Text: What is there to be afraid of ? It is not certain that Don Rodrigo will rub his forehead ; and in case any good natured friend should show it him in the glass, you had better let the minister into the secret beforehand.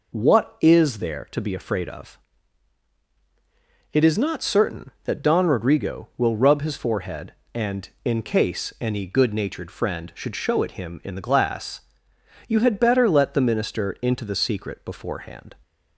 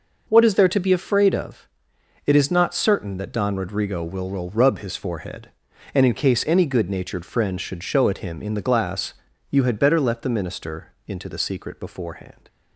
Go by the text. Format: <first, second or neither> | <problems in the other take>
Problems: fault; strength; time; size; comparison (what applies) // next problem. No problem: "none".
first | says "will" twice; at 4.2 s